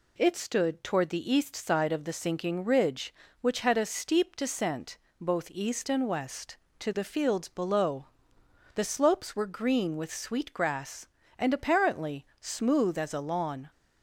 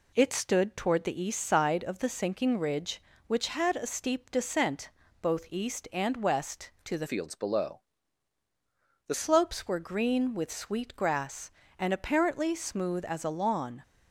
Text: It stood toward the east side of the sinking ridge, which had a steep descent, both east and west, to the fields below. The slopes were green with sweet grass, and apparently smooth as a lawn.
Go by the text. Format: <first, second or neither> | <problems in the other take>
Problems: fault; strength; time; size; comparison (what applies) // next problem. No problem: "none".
first | changes voice from "fields" to "The"; from 7.0 to 9.1 s; 2.1 s long